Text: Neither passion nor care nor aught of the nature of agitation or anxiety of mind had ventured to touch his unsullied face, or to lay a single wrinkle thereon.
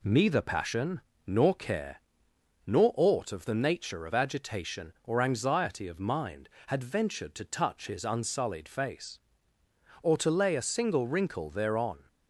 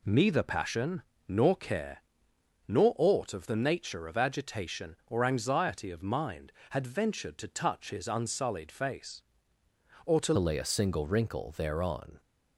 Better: first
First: pauses between "passion" and "nor"; slight; at 0.9 s; 0.28 s long // pauses between "care" and "nor"; noticeable; at 1.9 s; 0.66 s long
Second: pauses between "passion" and "nor"; slight; at 1.0 s; 0.28 s long // pauses between "care" and "nor"; noticeable; at 2.0 s; 0.66 s long // changes voice at "lay"; from 10.3 s on; 1.8 s long

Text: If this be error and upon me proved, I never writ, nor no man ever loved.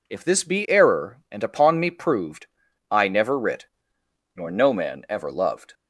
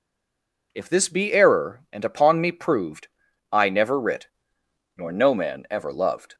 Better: first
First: none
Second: stays silent before the first word; slight; until 0.7 s; 0.7 s long

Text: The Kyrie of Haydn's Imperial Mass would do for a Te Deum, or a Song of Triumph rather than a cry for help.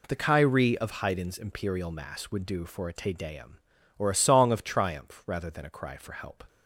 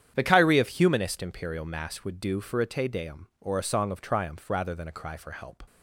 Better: first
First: none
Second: starts louder than the rest; strong; until 1.1 s; 9.5 dB // says "Humanist" for "Haydn's"; at 0.6 s

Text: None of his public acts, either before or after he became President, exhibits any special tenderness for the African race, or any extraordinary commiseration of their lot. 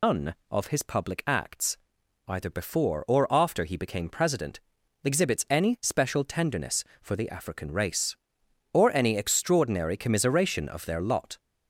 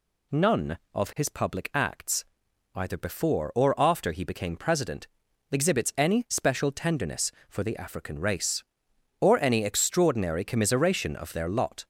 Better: second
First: loses the start of "None"; at 0.0 s; 155 ms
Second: none

